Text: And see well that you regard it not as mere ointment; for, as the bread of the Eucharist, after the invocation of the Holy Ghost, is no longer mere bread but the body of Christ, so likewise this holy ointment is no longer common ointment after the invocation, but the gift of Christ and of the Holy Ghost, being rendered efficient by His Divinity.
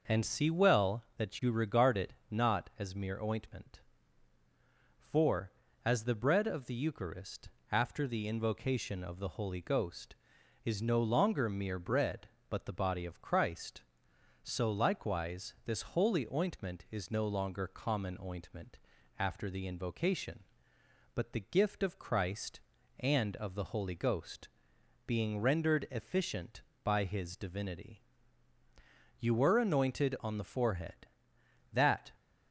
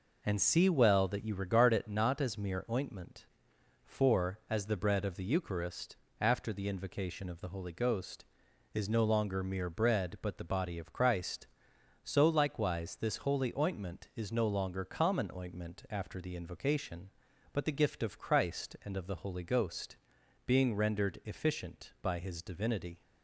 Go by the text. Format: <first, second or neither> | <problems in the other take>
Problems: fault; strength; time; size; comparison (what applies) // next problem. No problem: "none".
second | pauses between "it" and "not"; slight; at 2.1 s; 0.16 s long // pauses between "ointment" and "after"; at 18.7 s; 0.40 s long // goes on to say "You were anointed on the forehead that"; strong; from 29.2 s on; 2.9 s long